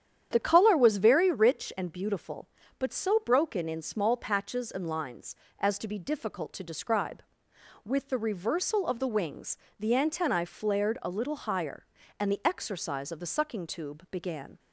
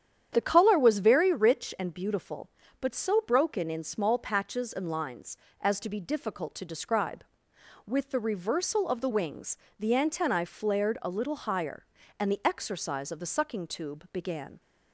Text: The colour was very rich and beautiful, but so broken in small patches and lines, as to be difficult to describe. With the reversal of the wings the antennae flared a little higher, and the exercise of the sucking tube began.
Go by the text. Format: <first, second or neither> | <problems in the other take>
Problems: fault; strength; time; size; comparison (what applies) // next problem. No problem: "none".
neither | starts louder than the rest; strong; the same in both // pauses between "wings" and "the"; slight; the same in both